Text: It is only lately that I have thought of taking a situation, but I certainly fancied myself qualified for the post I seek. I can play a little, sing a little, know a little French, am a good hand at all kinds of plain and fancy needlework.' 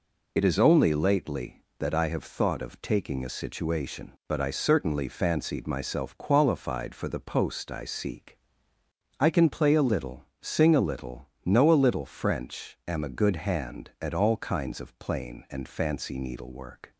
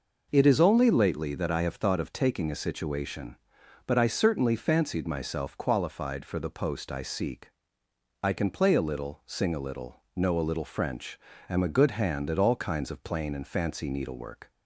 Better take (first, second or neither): second